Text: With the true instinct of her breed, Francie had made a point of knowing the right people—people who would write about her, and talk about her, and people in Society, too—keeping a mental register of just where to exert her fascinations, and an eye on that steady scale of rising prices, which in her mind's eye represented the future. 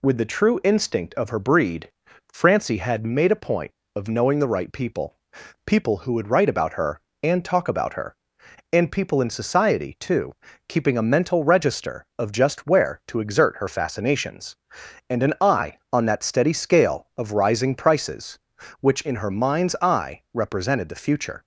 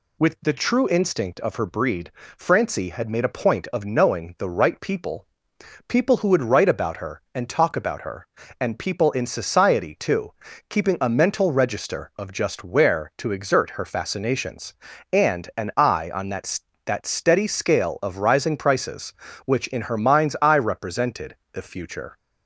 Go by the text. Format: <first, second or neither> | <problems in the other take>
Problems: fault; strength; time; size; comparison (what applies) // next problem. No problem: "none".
first | says "that" twice; at 16.8 s // pauses between "represented" and "the"; slight; at 21.3 s; 0.16 s long